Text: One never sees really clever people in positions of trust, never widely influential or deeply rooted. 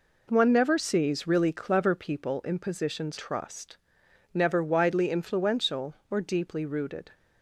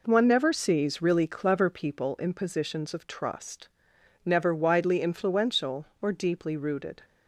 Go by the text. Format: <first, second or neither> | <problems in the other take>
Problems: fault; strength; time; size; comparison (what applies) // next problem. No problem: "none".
second | skips "of"; at 3.1 s